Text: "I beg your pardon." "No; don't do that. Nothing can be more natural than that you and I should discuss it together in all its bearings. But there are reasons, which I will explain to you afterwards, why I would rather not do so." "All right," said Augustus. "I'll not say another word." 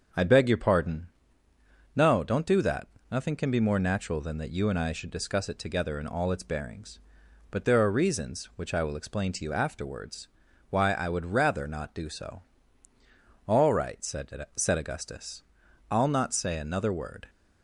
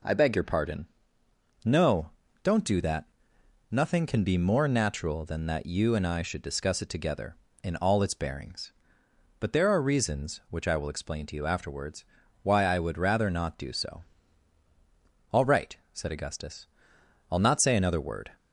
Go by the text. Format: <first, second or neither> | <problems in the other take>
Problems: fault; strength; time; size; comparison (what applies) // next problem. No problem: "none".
second | starts louder than the rest; until 2.0 s; 6.5 dB // says "said" twice; at 14.5 s